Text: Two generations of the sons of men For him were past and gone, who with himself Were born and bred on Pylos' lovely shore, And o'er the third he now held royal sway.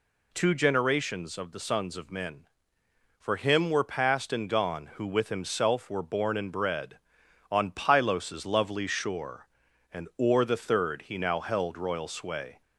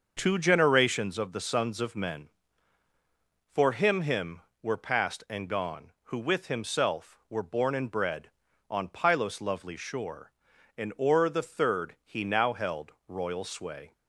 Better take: first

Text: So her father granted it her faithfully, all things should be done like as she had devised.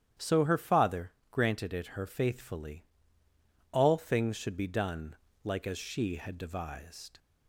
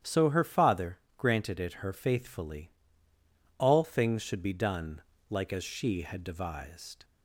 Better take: neither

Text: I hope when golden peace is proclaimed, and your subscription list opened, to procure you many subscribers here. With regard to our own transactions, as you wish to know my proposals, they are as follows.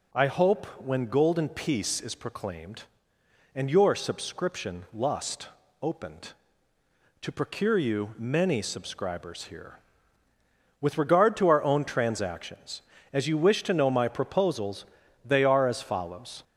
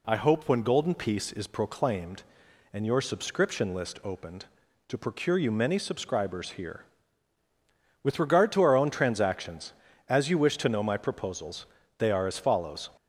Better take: second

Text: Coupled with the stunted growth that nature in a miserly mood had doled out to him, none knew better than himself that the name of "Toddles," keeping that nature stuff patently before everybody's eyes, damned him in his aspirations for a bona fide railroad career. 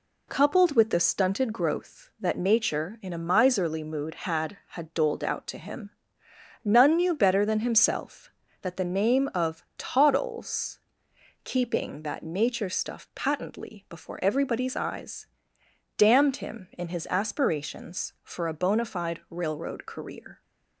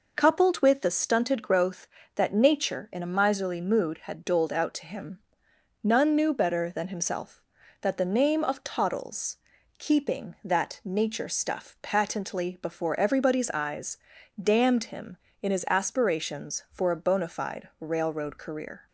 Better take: second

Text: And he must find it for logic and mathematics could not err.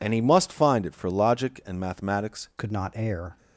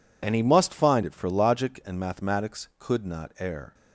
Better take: second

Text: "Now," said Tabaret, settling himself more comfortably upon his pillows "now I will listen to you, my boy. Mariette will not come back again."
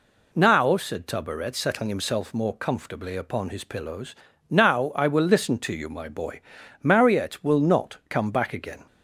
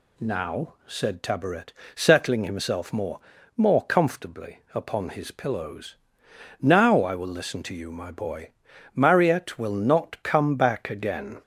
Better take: first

